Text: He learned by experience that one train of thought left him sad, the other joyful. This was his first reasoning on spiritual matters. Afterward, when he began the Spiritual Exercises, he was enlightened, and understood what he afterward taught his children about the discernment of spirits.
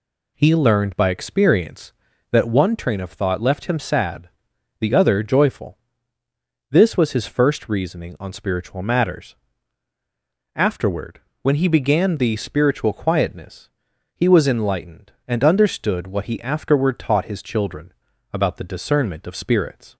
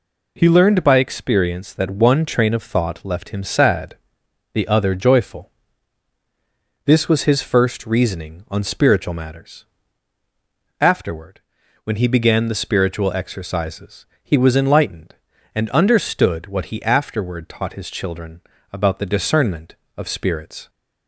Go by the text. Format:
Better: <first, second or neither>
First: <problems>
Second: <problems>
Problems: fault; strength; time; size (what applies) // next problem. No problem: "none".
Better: second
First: says "Quietness" for "Exercises"; at 12.9 s // pauses between "children" and "about"; at 17.9 s; 0.40 s long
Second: pauses between "children" and "about"; slight; at 18.4 s; 0.30 s long